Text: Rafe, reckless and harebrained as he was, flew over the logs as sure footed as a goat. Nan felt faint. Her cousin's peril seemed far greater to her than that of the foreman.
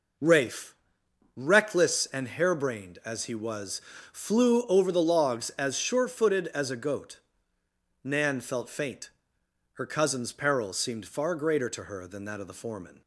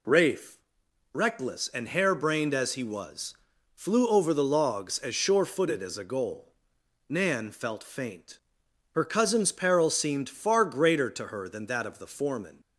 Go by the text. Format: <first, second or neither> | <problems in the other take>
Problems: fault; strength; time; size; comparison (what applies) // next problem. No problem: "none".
first | says "goal" for "goat"; at 6.0 s